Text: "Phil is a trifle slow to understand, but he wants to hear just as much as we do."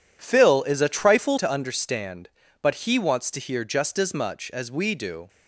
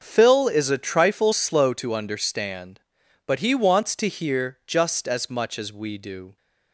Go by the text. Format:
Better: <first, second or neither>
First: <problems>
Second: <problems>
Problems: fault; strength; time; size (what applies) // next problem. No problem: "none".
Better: second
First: skips "slow"; at 1.3 s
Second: none